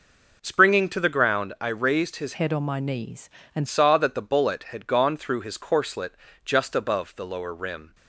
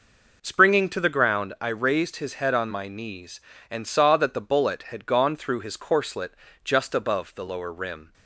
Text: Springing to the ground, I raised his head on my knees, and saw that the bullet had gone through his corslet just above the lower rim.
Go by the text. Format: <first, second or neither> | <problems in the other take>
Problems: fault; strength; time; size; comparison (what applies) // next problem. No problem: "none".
second | changes voice from "head" to "and"; from 2.3 to 3.6 s; 1.3 s long // pauses between "corslet" and "just"; slight; at 6.1 s; 0.32 s long; slight in the second